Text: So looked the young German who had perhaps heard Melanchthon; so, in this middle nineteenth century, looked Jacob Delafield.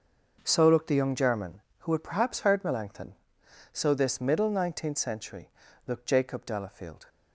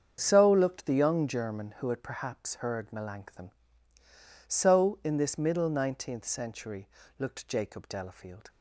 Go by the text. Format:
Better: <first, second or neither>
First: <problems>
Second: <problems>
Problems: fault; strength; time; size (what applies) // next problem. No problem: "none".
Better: second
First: starts louder than the rest; noticeable; until 1.4 s; 6 dB // skips "in"; at 3.9 s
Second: starts louder than the rest; strong; until 1.2 s; 7.5 dB